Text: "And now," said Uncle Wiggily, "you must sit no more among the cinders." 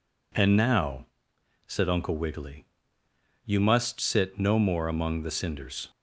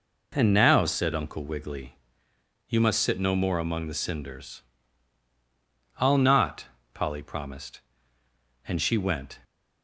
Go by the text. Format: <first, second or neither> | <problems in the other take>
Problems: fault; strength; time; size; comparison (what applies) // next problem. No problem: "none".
first | goes on to say "I'll not Polly promised and she went"; strong; from 5.9 s on; 3.4 s long